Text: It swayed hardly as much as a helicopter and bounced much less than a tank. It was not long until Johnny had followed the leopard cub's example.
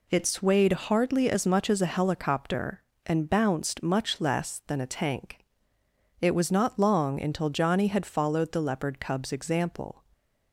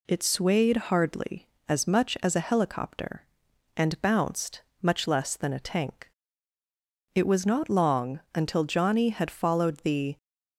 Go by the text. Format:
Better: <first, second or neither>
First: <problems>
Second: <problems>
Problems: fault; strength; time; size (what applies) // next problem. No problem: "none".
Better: first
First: none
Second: pauses between "bounced" and "much"; slight; at 4.6 s; 0.20 s long // pauses between "long" and "until"; slight; at 8.1 s; 0.16 s long // stops before "leopard cub's example"; at 10.1 s